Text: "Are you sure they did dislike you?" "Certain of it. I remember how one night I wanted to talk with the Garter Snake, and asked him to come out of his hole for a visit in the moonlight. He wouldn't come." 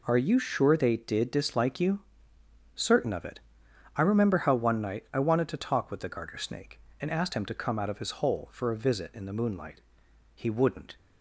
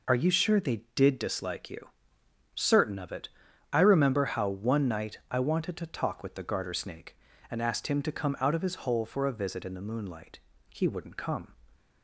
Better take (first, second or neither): second